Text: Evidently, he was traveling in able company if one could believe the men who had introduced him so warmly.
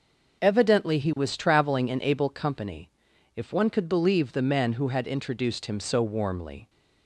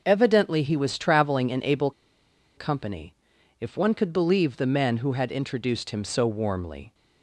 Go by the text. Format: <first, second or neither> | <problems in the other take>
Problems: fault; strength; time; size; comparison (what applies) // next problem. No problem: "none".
first | pauses between "able" and "company"; noticeable; at 1.9 s; 0.65 s long // pauses between "company" and "if"; noticeable; at 3.1 s; 0.48 s long; noticeable in the first